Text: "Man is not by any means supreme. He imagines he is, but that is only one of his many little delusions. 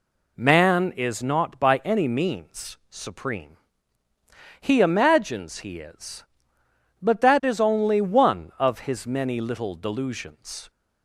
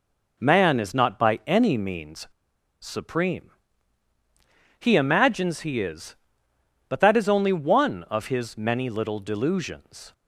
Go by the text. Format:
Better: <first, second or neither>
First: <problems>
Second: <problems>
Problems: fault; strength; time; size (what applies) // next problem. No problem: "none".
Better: first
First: none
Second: pauses between "means" and "supreme"; noticeable; at 2.2 s; 0.53 s long